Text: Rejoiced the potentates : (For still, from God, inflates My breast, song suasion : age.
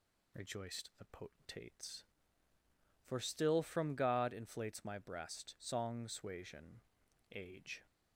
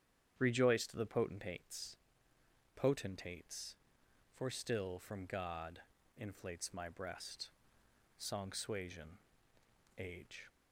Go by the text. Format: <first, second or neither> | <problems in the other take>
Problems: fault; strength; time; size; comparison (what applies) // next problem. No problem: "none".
first | starts louder than the rest; strong; until 1.3 s; 9.5 dB // says "potentates" twice; at 2.7 s